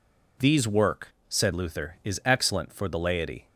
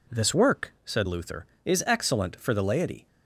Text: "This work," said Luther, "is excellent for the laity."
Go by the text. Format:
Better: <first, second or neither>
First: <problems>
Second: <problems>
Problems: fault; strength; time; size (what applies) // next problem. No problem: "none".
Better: second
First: says "These" for "This"; at 0.3 s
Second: none